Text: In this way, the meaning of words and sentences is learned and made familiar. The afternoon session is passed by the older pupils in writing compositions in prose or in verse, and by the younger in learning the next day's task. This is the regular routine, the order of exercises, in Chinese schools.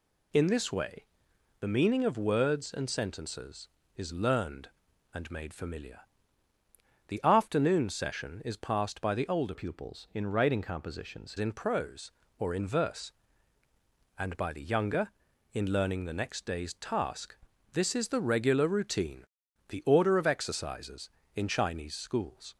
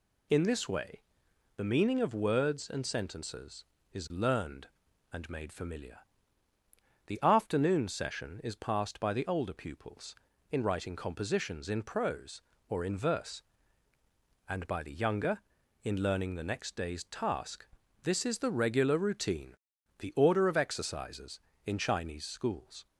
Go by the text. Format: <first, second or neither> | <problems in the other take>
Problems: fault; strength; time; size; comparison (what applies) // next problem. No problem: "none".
second | changes voice from "pupils" to "compositions"; from 9.5 to 11.3 s; 1.8 s long